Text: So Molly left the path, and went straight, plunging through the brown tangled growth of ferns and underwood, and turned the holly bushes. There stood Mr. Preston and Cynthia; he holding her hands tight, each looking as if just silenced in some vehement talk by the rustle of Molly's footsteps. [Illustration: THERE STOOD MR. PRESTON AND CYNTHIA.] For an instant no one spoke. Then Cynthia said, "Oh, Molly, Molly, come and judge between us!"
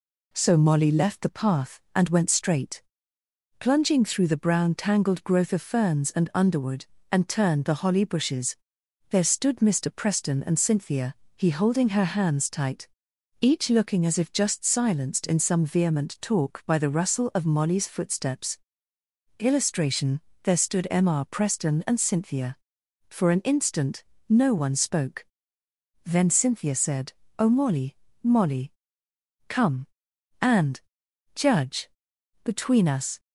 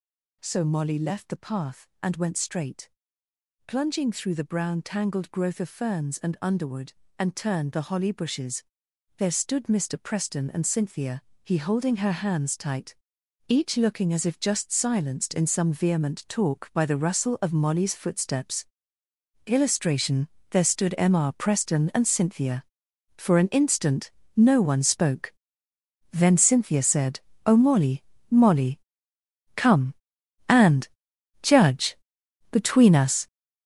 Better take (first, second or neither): first